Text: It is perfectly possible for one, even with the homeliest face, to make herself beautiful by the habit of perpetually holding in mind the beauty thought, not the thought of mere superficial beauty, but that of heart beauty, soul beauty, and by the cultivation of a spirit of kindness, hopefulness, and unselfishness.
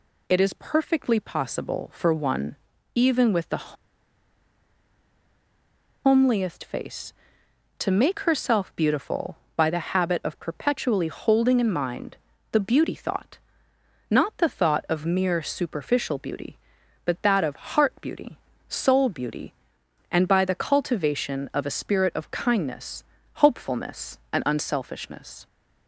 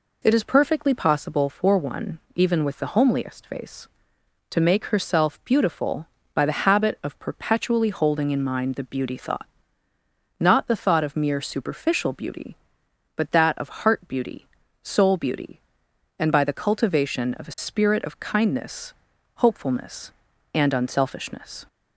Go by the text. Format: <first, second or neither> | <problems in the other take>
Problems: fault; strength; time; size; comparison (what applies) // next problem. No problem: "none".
second | pauses between "the" and "homeliest"; strong; at 3.7 s; 2.2 s long // pauses between "mind" and "the"; slight; at 12.1 s; 0.36 s long